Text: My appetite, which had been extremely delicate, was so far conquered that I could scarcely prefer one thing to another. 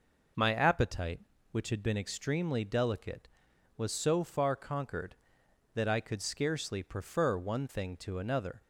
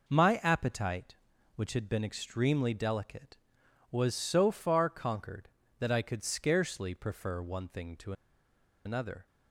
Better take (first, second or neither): first